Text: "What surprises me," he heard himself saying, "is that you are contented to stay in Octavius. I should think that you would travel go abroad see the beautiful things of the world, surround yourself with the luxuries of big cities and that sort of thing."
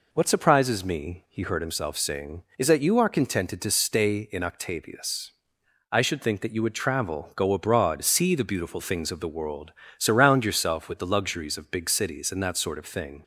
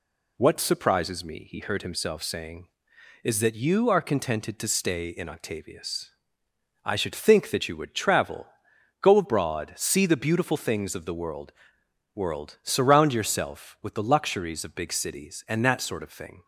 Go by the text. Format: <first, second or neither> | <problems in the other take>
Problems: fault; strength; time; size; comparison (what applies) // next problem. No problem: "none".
first | pauses between "travel" and "go"; noticeable; at 8.4 s; 0.54 s long // says "world" twice; at 12.1 s